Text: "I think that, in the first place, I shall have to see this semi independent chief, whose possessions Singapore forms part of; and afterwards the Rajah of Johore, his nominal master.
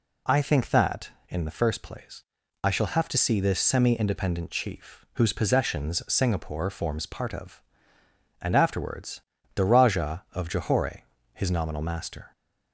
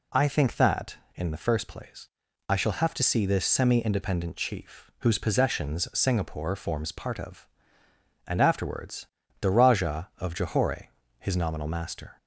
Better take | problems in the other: neither | pauses between "afterwards" and "the"; slight; the same in both

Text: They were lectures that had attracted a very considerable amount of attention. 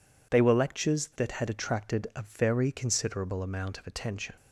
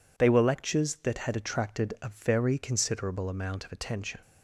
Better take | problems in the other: neither | none

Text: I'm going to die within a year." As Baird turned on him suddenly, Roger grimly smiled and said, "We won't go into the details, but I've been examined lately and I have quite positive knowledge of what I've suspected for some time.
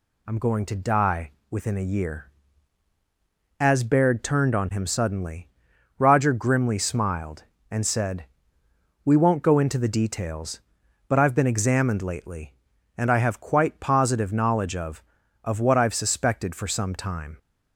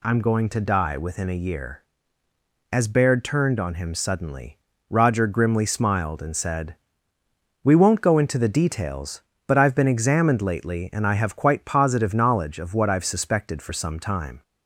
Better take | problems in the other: second | pauses between "die" and "within"; slight; at 1.3 s; 0.18 s long // says "of" twice; at 15.4 s

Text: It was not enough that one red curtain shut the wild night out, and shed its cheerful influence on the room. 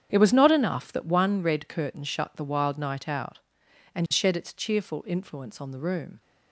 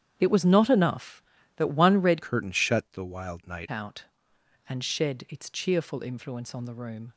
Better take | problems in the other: first | starts louder than the rest; strong; until 1.1 s; 9.5 dB; strong in the first // changes voice from "curtain" to "night"; from 2.2 to 3.6 s; 1.4 s long

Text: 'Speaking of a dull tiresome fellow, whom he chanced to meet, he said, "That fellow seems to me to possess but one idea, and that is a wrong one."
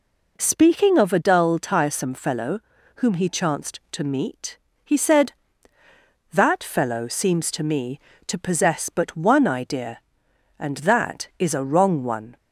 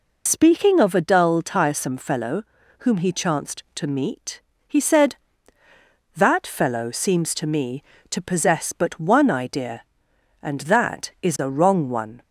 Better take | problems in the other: first | loses the start of "Speaking"; at 0.2 s; 60 ms

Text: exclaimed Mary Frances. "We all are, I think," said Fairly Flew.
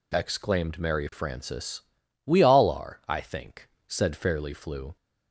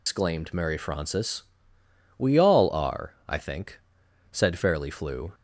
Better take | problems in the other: first | loses the start of "exclaimed"; at 0.0 s; 150 ms

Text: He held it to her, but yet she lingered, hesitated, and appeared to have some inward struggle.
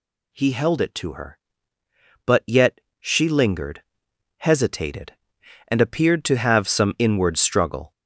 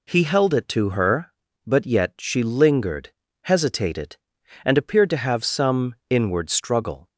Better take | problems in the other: second | gets louder; throughout; 6.5 dB // pauses between "yet" and "she"; slight; at 2.7 s; 0.20 s long

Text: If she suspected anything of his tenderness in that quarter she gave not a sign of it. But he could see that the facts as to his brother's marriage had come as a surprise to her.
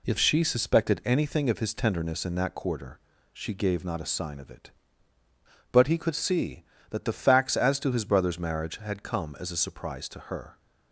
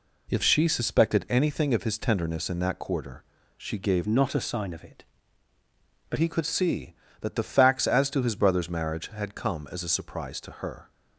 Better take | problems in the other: first | pauses between "quarter" and "she"; slight; at 3.2 s; 0.34 s long; slight in the first // changes voice from "not" to "But"; from 4.0 to 6.1 s; 2.1 s long

